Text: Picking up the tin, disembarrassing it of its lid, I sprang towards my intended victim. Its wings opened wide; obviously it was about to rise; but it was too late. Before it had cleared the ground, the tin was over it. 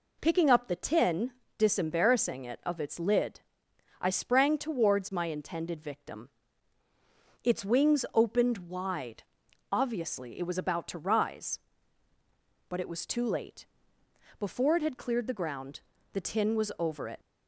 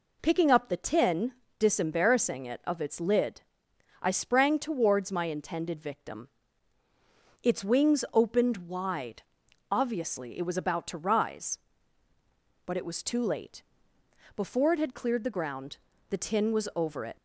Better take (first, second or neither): neither